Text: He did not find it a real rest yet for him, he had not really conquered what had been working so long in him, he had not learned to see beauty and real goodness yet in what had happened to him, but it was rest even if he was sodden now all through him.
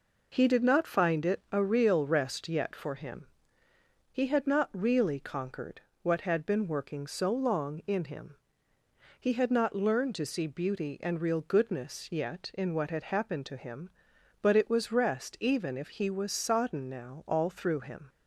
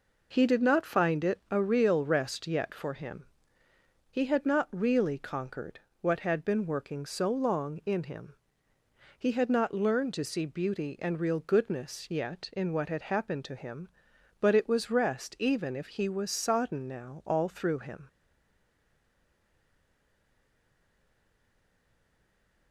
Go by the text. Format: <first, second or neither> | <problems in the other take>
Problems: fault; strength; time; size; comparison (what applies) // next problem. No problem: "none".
first | pauses between "conquered" and "what"; slight; at 5.7 s; 0.20 s long; slight in the first // stays silent after the last word; strong; from 18.0 s on; 4.7 s long